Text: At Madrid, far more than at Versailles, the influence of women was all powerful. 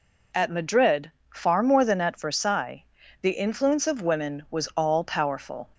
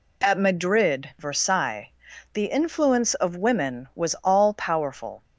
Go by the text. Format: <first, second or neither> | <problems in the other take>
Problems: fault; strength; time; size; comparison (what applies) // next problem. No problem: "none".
first | skips "far more than at"; at 1.1 s